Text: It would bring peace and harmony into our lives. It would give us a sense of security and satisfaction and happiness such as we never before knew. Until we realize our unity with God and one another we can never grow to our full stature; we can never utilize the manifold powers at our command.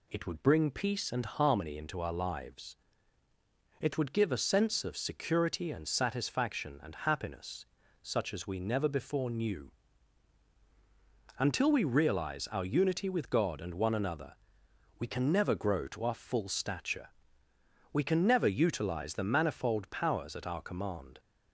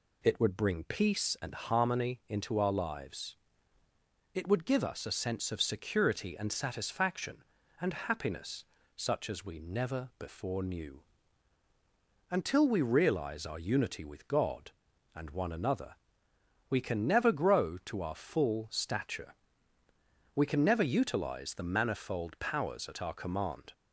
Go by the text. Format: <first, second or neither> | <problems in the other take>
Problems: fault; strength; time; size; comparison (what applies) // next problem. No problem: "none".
second | skips "us"; at 4.3 s // pauses between "happiness" and "such"; slight; at 7.6 s; 0.36 s long; slight in the second // pauses between "another" and "we"; noticeable; at 14.3 s; 0.66 s long; noticeable in the second